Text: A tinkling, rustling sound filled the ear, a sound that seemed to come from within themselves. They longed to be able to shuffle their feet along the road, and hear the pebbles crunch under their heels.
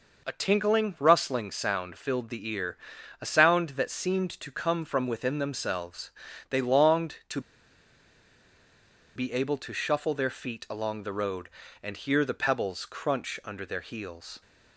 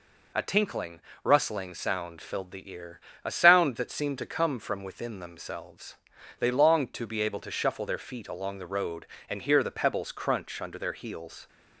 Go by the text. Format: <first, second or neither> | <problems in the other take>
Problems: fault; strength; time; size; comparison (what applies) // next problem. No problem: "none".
second | pauses between "to" and "be"; strong; at 7.3 s; 1.7 s long